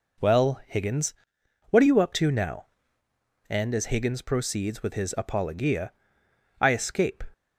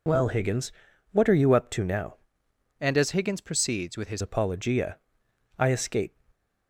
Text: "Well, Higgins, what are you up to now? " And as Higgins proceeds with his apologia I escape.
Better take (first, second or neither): first